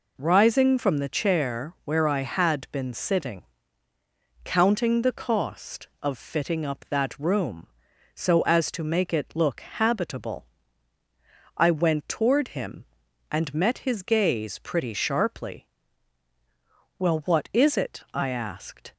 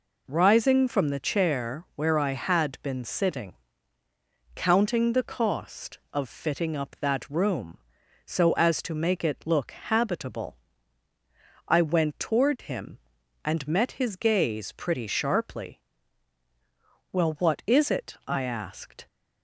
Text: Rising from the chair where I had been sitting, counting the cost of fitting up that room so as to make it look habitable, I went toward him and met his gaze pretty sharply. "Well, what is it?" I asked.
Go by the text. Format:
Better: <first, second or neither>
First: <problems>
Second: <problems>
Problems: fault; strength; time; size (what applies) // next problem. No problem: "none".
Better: neither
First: none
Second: none